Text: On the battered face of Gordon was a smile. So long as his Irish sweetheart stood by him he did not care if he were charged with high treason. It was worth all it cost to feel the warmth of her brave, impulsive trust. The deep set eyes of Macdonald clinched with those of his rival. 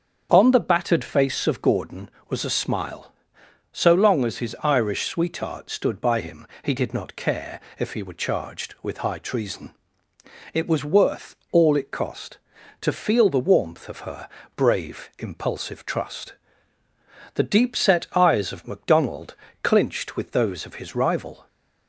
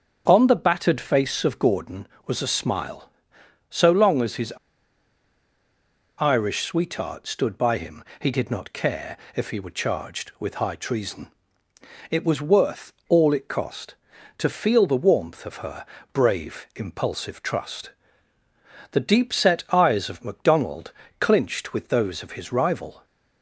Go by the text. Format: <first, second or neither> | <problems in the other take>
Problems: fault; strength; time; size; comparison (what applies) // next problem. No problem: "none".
first | starts louder than the rest; strong; until 1.2 s; 7.5 dB; strong in the first // pauses between "his" and "Irish"; strong; at 4.5 s; 1.6 s long // pauses between "him" and "he"; slight; at 8.0 s; 0.18 s long; slight in the first // pauses between "care" and "if"; slight; at 9.1 s; 0.20 s long; slight in the first // pauses between "worth" and "all"; slight; at 12.9 s; 0.16 s long; slight in the first // pauses between "her" and "brave"; slight; at 15.8 s; 0.26 s long; slight in the first // pauses between "Macdonald" and "clinched"; slight; at 20.8 s; 0.30 s long; slight in the first